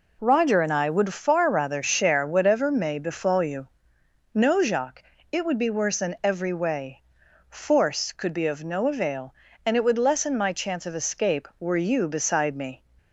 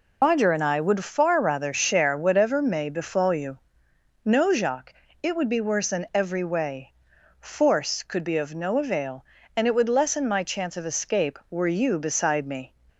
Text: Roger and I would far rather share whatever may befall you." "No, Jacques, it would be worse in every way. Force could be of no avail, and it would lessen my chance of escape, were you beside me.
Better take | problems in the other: first | loses the start of "Roger"; at 0.2 s; 120 ms

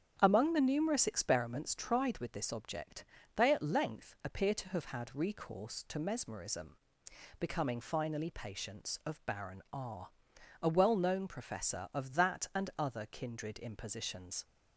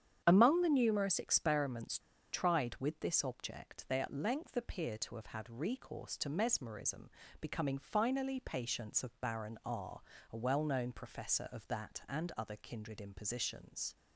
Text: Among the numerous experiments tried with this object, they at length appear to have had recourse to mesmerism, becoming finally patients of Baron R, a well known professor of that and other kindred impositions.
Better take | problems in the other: first | starts louder than the rest; strong; until 1.2 s; 9 dB; strong in the first // pauses between "experiments" and "tried"; slight; at 1.9 s; 0.33 s long

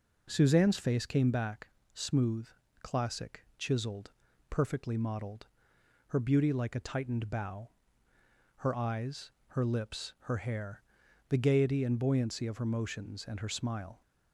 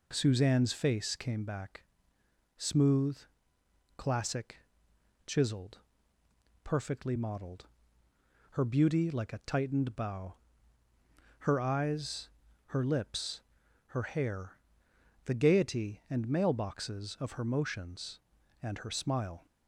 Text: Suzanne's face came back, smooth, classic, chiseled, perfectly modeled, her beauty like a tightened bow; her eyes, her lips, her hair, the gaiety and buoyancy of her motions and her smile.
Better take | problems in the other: first | says "mailboxes" for "buoyancy"; at 16.2 s

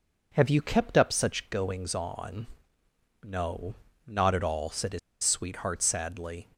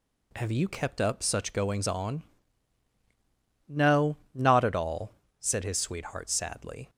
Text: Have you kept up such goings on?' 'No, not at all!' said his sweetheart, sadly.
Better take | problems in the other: second | pauses between "his" and "sweetheart"; slight; at 4.9 s; 0.24 s long

